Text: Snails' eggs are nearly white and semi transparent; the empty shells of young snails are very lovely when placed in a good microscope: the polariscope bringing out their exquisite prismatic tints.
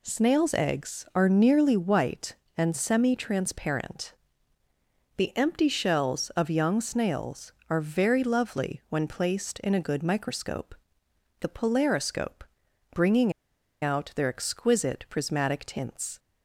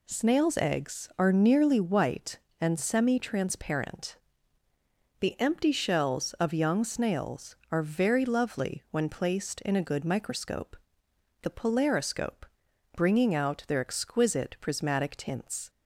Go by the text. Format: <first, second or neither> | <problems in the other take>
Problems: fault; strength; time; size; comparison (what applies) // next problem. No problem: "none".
second | pauses between "polariscope" and "bringing"; noticeable; at 12.4 s; 0.50 s long; noticeable in the second // pauses between "bringing" and "out"; noticeable; at 13.3 s; 0.50 s long